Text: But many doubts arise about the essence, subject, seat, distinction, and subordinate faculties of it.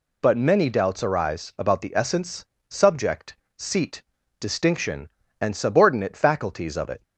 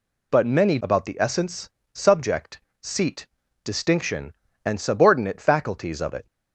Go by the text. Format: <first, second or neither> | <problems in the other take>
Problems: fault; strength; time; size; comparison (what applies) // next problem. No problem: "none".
first | skips "doubts arise"; at 0.8 s